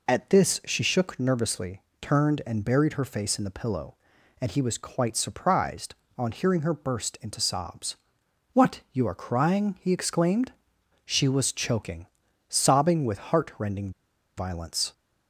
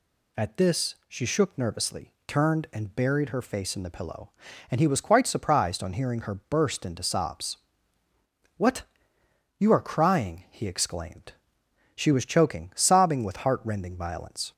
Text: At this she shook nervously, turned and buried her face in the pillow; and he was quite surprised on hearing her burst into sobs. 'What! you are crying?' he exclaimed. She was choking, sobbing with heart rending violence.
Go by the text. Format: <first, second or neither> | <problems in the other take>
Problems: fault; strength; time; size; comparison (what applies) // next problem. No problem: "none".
second | pauses between "rending" and "violence"; noticeable; at 13.9 s; 0.47 s long